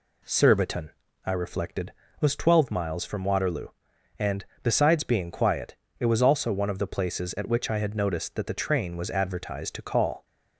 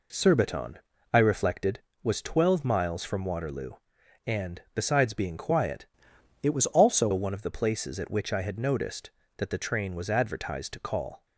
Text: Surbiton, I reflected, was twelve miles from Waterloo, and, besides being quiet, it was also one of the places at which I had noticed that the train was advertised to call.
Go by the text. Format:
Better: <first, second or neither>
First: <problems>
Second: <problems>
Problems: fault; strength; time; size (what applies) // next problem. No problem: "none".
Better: first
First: none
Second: changes voice from "it" to "also"; from 6.4 to 7.0 s; 0.6 s long